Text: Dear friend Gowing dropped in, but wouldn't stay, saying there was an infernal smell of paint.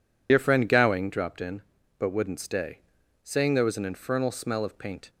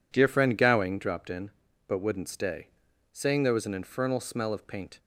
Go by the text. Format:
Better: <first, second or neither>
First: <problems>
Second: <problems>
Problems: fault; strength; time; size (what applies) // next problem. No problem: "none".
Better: second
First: loses the start of "Dear"; at 0.2 s; 65 ms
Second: none